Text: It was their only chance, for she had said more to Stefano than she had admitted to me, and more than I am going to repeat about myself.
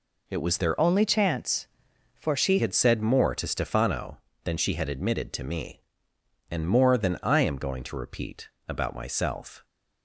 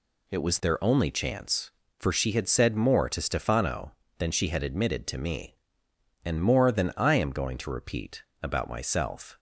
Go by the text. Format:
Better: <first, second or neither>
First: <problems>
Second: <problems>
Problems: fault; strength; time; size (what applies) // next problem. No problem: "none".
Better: second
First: changes voice from "only" to "she"; from 0.7 to 2.5 s; 1.8 s long // pauses between "repeat" and "about"; slight; at 8.4 s; 0.20 s long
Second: pauses between "repeat" and "about"; slight; at 8.2 s; 0.20 s long